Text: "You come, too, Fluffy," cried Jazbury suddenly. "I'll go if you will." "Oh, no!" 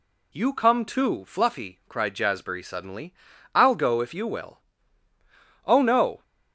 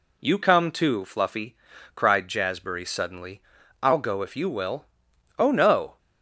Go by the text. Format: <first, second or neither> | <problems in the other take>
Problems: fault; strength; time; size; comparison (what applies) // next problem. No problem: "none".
neither | none